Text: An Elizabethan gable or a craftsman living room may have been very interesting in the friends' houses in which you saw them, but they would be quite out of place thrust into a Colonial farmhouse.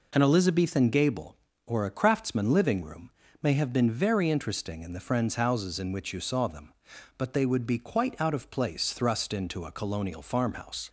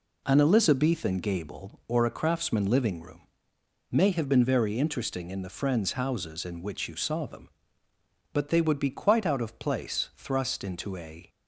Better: first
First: pauses between "room" and "may"; slight; at 3.1 s; 0.32 s long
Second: pauses between "room" and "may"; noticeable; at 3.2 s; 0.68 s long // stops before "Colonial farmhouse"; at 11.2 s

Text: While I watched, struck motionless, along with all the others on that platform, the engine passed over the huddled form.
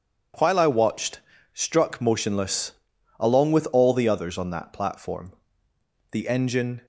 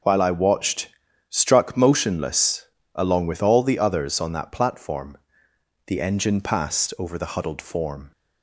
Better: second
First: stops before "passed over the huddled form"; at 6.8 s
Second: none

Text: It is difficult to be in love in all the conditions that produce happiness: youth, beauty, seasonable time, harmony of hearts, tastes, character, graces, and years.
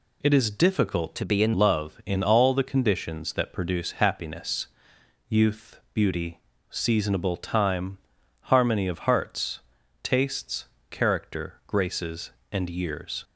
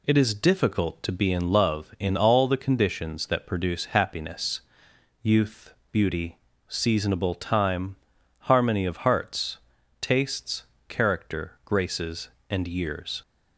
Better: second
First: changes voice from "to" to "in"; from 1.1 to 1.5 s; 0.4 s long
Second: none

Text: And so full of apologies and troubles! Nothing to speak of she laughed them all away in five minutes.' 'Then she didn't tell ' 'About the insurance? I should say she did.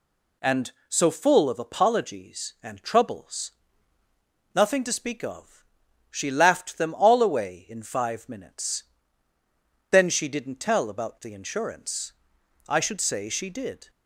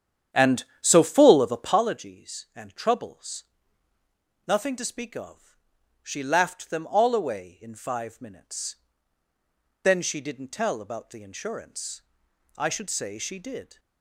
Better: first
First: pauses between "of" and "she"; noticeable; at 5.6 s; 0.46 s long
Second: starts louder than the rest; strong; until 1.9 s; 9.5 dB // pauses between "of" and "she"; noticeable; at 5.5 s; 0.46 s long

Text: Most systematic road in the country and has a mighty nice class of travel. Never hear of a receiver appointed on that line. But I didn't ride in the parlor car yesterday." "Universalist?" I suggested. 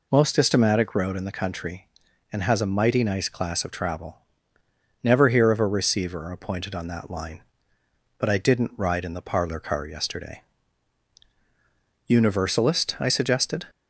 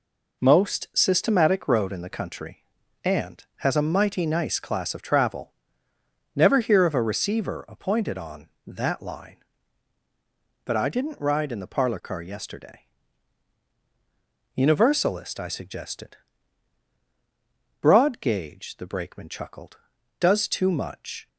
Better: first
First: none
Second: goes on to say "Broad gauge the Brakeman chuckled does too much"; strong; from 17.8 s on; 3.4 s long

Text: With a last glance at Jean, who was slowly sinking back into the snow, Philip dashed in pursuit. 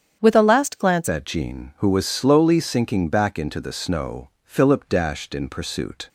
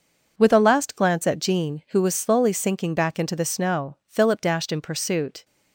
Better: second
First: starts louder than the rest; strong; until 1.2 s; 8.5 dB // changes voice at "at"; from 1.0 s on; 5.0 s long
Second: none

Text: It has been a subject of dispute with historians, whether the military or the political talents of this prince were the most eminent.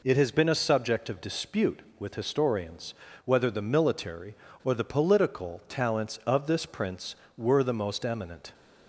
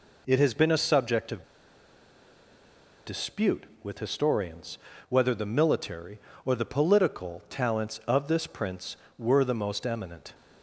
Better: first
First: none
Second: pauses between "of" and "dispute"; strong; at 1.4 s; 1.6 s long

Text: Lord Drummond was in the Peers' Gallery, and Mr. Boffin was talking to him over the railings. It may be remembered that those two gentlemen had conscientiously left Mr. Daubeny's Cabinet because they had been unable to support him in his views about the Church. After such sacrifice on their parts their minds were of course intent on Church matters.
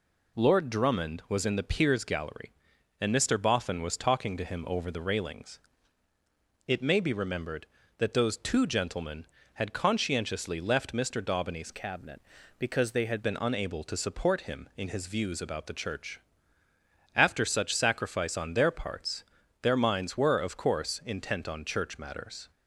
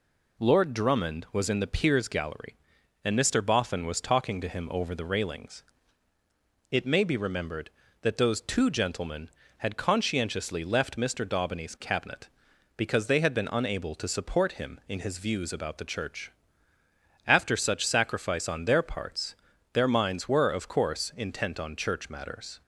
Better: second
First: changes voice from "Cabinet" to "had"; from 11.7 to 13.2 s; 1.5 s long // pauses between "parts" and "their"; at 19.2 s; 0.38 s long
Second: pauses between "parts" and "their"; at 19.3 s; 0.38 s long

